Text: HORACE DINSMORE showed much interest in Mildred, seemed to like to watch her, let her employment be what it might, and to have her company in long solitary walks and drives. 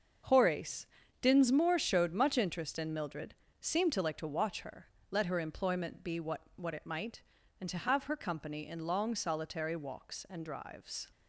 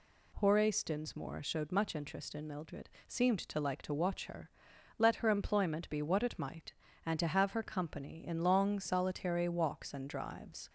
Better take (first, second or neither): second